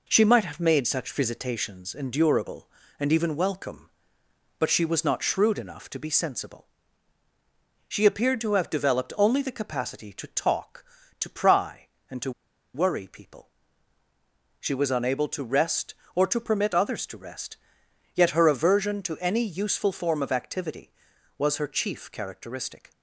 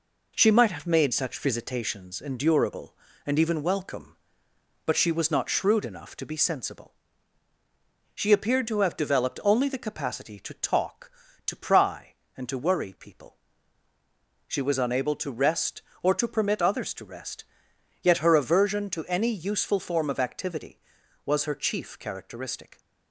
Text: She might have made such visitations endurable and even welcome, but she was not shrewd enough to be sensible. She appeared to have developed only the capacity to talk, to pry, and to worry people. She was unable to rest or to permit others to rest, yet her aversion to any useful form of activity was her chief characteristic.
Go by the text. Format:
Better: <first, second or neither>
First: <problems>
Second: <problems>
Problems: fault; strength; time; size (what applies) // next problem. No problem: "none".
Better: second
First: pauses between "to" and "worry"; at 12.3 s; 0.43 s long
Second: none